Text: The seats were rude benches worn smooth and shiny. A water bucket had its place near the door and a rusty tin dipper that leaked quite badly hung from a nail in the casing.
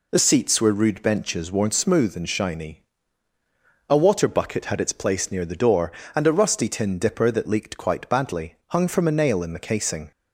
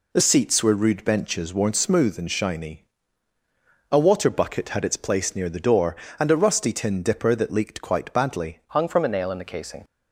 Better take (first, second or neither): first